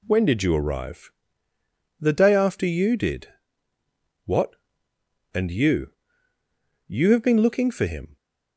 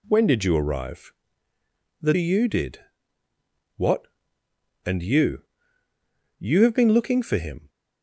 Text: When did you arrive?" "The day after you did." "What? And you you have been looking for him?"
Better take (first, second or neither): first